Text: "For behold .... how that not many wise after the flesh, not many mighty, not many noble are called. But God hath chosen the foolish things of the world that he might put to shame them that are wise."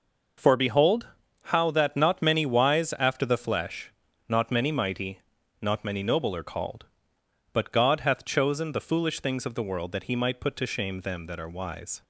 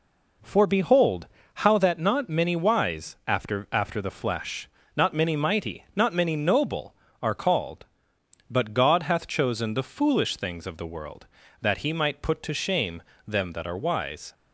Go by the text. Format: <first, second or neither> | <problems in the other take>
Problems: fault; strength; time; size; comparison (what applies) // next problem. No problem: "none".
first | says "after" twice; at 3.7 s // pauses between "shame" and "them"; slight; at 13.0 s; 0.24 s long